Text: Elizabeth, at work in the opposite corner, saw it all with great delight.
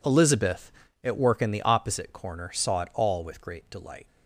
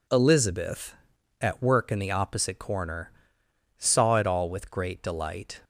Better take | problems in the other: neither | none

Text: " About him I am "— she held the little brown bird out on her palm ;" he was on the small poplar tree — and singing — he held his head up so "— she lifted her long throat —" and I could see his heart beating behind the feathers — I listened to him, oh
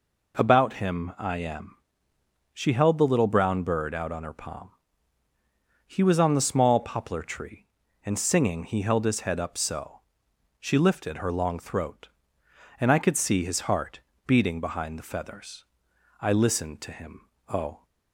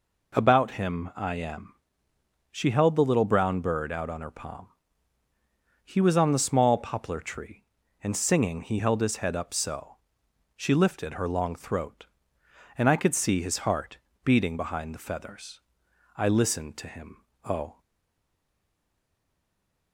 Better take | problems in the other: first | pauses between "heart" and "beating"; slight; at 13.9 s; 0.26 s long; slight in the first // stays silent after the last word; from 17.8 s on; 2.1 s long

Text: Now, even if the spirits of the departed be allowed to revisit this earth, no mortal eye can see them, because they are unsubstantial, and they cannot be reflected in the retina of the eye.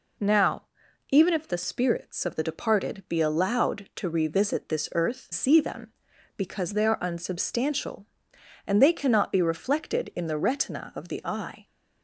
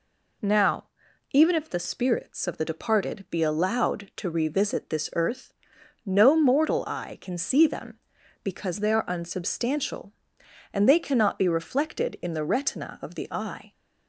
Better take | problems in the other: second | skips "no mortal eye can"; at 5.3 s

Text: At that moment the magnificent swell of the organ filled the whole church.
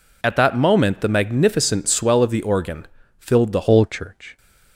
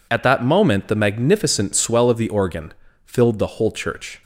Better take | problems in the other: second | pauses between "organ" and "filled"; slight; at 2.8 s; 0.34 s long; slight in the second // changes voice at "whole"; from 3.6 s on; 0.7 s long

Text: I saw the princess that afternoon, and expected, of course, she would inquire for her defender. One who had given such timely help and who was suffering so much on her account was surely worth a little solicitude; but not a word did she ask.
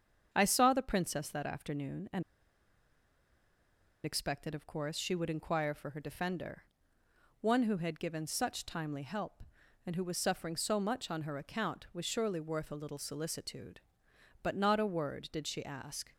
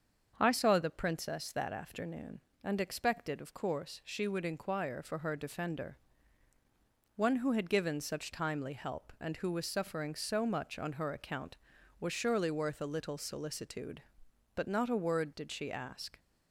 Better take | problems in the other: second | starts louder than the rest; strong; until 1.3 s; 7.5 dB; also in the second // pauses between "and" and "expected"; strong; at 2.2 s; 1.8 s long

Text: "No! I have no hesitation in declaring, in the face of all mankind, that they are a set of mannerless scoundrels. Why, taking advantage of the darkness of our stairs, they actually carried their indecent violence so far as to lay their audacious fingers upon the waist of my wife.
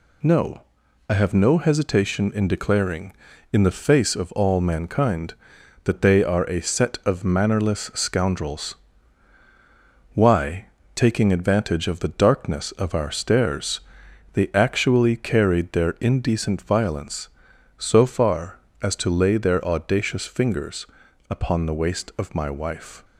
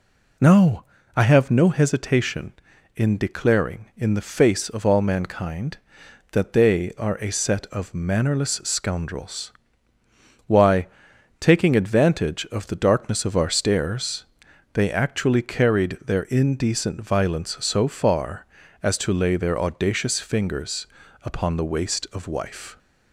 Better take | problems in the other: first | pauses between "fingers" and "upon"; at 20.8 s; 0.38 s long; noticeable in the first // skips "my"; at 22.2 s

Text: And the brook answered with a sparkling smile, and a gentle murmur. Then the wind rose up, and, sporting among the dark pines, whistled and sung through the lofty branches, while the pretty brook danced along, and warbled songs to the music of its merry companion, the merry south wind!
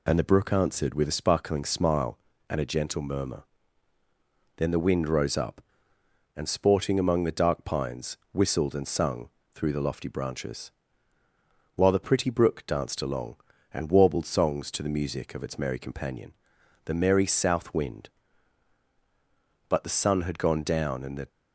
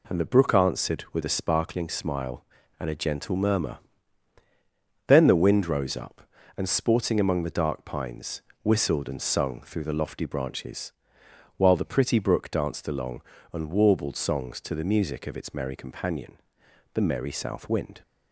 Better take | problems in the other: second | pauses between "sung" and "through"; slight; at 9.2 s; 0.26 s long // goes on to say "But the sun had gone down and the"; from 19.6 s on; 1.6 s long

